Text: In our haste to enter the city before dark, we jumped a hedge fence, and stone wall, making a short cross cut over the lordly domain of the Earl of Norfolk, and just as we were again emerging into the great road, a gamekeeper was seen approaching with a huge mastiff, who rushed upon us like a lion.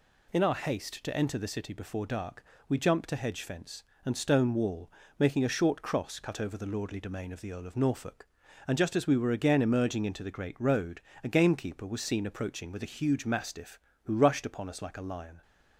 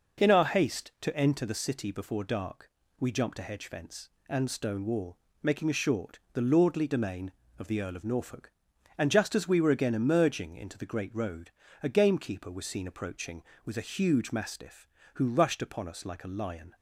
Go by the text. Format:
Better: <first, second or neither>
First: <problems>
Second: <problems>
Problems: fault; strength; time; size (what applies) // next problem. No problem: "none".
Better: first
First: none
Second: skips "cross cut over"; at 6.2 s